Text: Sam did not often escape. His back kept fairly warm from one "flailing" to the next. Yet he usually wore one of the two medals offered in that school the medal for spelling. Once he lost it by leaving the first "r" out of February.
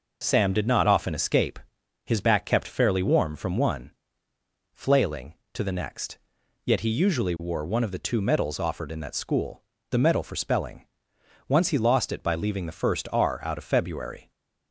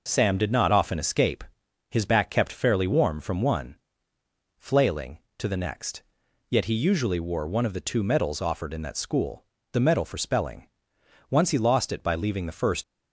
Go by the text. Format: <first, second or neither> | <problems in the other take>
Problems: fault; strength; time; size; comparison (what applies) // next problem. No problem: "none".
first | pauses between "one" and "flailing"; noticeable; at 3.7 s; 0.82 s long; noticeable in the first // pauses between "school" and "the"; slight; at 9.4 s; 0.30 s long; slight in the first // stops before "r out of February"; at 12.8 s